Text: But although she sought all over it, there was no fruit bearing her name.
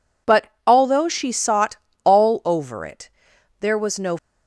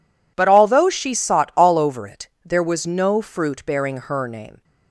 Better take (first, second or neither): second